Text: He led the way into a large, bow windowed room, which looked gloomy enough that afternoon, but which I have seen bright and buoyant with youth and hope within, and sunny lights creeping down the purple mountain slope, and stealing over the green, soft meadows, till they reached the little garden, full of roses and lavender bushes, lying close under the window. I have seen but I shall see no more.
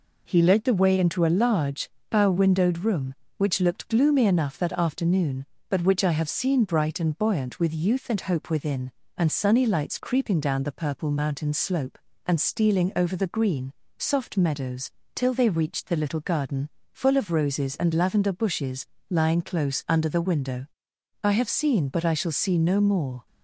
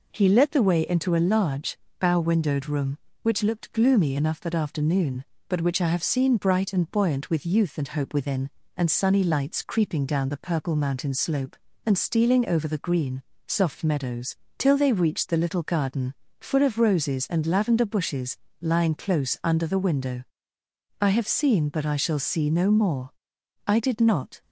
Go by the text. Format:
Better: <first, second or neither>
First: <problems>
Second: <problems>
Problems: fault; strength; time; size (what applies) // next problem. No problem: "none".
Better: first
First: none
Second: goes on to say "I did not"; noticeable; from 23.6 s on; 0.76 s long